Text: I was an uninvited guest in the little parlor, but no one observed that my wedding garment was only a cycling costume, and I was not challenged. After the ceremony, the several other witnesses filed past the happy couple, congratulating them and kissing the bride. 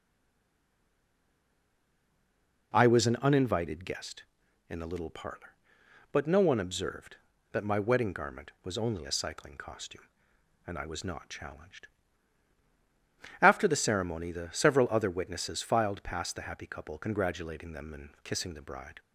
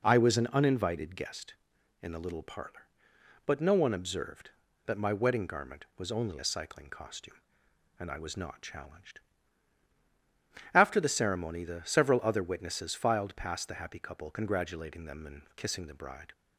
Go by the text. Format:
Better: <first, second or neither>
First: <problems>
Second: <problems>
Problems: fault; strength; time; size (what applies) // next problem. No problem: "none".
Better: second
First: stays silent before the first word; strong; until 2.7 s; 2.7 s long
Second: none